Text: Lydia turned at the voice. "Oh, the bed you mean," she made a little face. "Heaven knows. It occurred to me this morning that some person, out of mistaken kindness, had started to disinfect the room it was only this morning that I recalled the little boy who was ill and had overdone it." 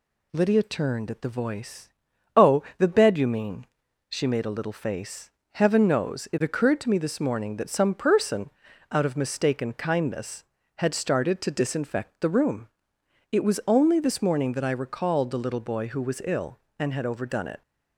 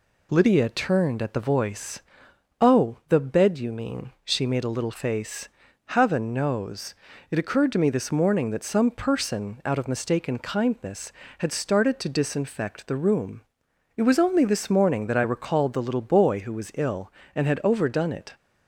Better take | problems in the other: neither | pauses between "room" and "it"; noticeable; the same in both

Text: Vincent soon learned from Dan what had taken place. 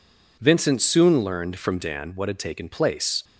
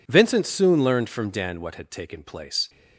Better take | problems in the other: neither | none

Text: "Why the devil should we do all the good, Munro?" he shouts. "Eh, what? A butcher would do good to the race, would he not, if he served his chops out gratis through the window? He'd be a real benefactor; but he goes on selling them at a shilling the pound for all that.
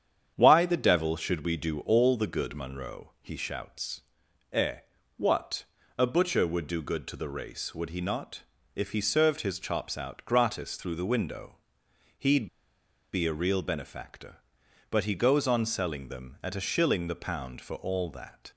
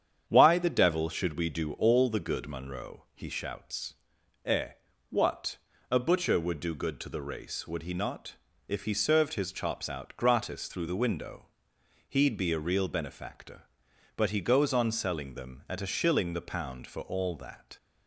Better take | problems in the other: second | starts louder than the rest; strong; until 1.3 s; 8.5 dB; strong in the second // pauses between "He'd" and "be"; noticeable; at 12.4 s; 0.65 s long

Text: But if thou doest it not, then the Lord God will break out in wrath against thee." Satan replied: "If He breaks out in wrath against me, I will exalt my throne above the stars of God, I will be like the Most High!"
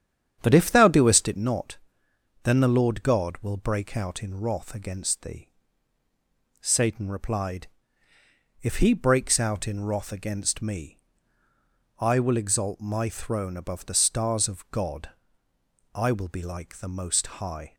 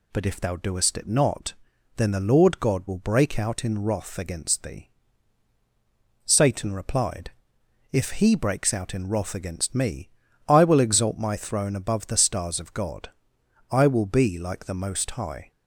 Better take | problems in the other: second | starts louder than the rest; strong; until 1.4 s; 9 dB // pauses between "Most" and "High"; slight; at 17.2 s; 0.16 s long

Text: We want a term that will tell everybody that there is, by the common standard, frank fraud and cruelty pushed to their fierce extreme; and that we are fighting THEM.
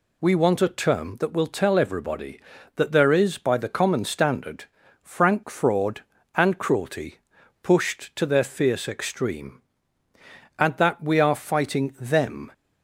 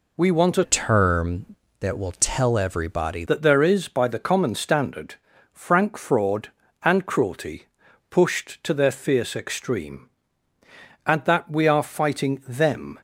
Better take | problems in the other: first | changes voice from "term" to "everybody"; from 0.6 to 3.2 s; 2.6 s long // pauses between "cruelty" and "pushed"; noticeable; at 7.6 s; 0.46 s long; noticeable in the first

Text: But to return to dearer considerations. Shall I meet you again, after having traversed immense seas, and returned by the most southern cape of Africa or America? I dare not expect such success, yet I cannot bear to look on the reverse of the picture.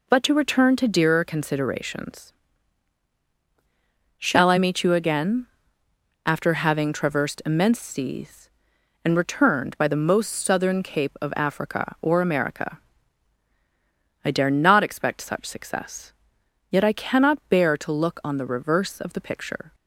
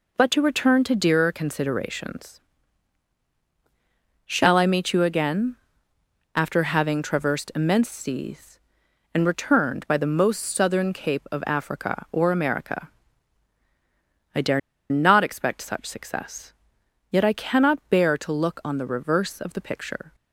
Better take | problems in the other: first | pauses between "dare" and "not"; slight; at 14.5 s; 0.30 s long

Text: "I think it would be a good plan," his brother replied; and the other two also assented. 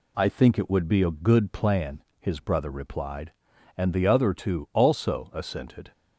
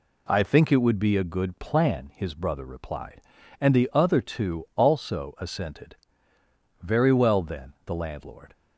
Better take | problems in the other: first | goes on to say "Very well then the landlord"; strong; from 6.8 s on; 1.7 s long

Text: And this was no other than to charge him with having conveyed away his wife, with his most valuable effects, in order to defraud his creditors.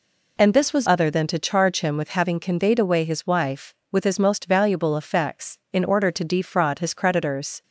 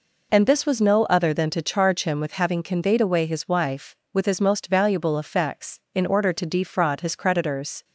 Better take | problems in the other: second | skips "no"; at 0.8 s

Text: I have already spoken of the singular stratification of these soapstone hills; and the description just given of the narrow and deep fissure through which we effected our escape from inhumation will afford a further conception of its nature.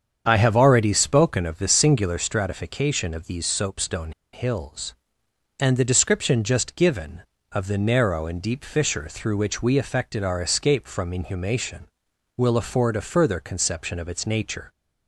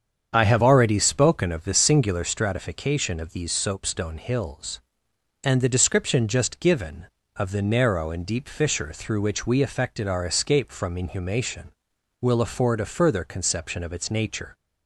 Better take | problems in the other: second | starts louder than the rest; strong; until 1.2 s; 7.5 dB; strong in the second // pauses between "soapstone" and "hills"; slight; at 4.1 s; 0.22 s long

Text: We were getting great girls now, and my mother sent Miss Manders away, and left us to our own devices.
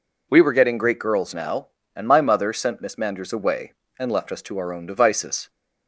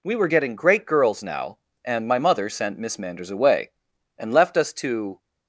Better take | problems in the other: first | stops before "our own devices"; at 5.1 s

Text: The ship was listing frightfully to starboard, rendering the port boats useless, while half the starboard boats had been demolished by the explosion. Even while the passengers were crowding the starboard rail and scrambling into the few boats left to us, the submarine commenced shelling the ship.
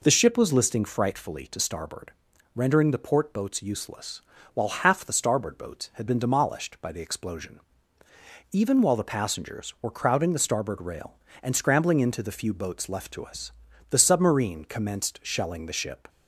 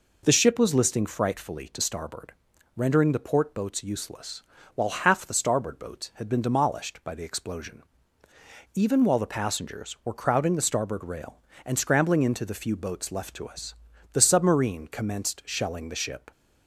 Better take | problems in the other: neither | none

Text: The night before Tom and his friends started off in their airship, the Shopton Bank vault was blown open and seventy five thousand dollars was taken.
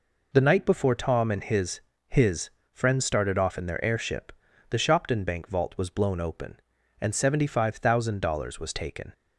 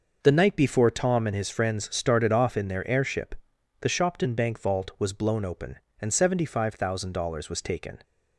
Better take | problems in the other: second | says "his" twice; at 2.0 s

